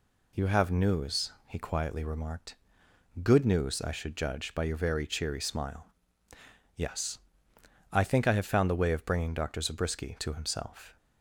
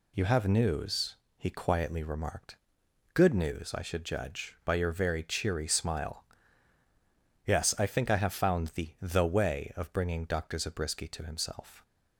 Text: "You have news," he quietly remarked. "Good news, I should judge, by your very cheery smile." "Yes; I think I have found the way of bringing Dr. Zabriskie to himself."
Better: first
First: none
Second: says "the" twice; at 9.0 s

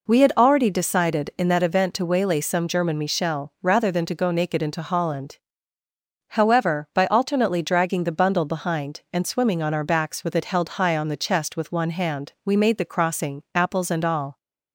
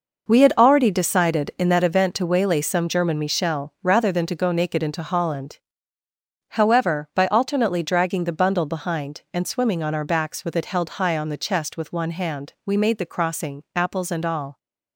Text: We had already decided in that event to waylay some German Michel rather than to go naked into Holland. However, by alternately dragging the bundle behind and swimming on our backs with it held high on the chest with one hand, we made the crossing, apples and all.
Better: first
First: none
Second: gets quieter; strong; throughout; 10 dB

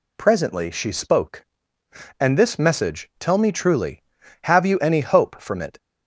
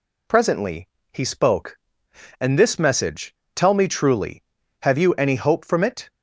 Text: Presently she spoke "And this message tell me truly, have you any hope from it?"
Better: first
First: none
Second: says "he" for "she"; at 1.1 s // pauses between "message" and "tell"; slight; at 3.3 s; 0.22 s long

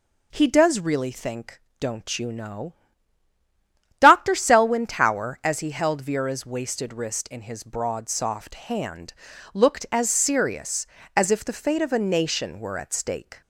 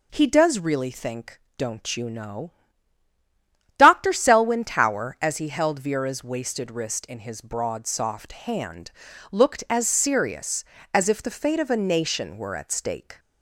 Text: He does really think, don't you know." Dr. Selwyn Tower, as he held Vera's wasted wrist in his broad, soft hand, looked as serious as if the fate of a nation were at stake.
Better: neither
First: none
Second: none

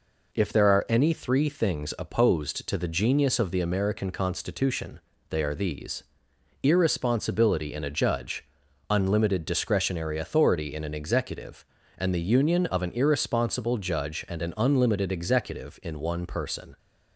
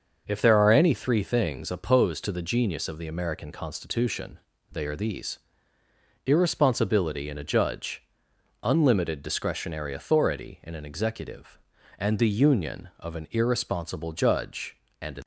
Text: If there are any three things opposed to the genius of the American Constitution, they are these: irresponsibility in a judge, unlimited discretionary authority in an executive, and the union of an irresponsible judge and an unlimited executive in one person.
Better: first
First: none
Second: starts louder than the rest; until 1.2 s; 6.5 dB // stops before "unlimited executive in one person"; at 15.2 s

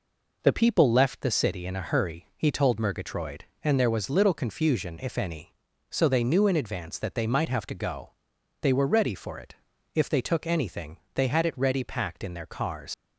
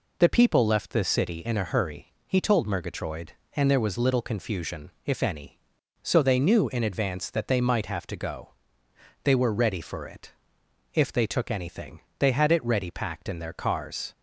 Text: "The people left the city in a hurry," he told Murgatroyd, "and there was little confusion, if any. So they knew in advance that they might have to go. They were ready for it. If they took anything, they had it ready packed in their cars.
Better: second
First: leaves "cars" unfinished; at 12.9 s; 100 ms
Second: none

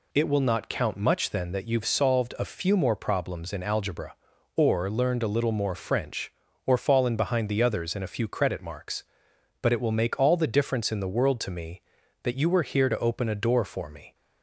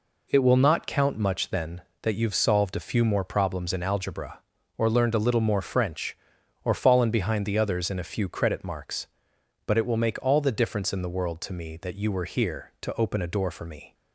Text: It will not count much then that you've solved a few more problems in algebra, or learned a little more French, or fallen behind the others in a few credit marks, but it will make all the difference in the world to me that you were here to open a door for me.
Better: neither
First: none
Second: none

